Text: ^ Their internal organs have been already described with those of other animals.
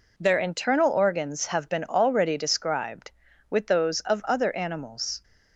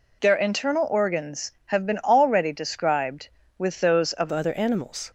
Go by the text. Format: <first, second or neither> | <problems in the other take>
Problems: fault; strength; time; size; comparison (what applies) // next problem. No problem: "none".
first | changes voice at "other"; from 4.3 s on; 0.8 s long